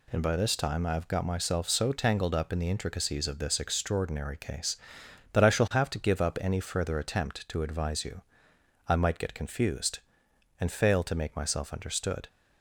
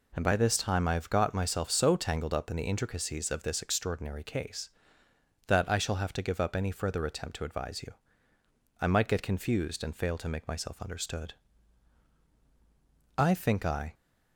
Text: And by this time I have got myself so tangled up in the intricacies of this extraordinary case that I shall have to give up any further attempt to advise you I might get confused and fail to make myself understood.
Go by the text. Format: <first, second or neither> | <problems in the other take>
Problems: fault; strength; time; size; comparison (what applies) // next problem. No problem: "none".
first | pauses between "you" and "I"; noticeable; at 7.9 s; 0.90 s long; noticeable in the first // goes on to say "I think I"; noticeable; from 13.1 s on; 0.76 s long